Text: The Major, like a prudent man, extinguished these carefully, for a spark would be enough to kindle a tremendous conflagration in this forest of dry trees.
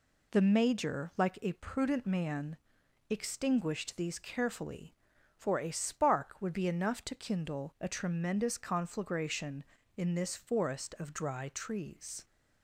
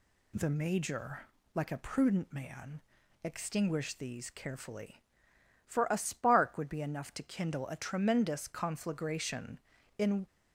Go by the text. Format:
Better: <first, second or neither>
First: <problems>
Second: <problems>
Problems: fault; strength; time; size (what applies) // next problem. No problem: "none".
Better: first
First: none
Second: stops before "this forest of dry trees"; at 10.2 s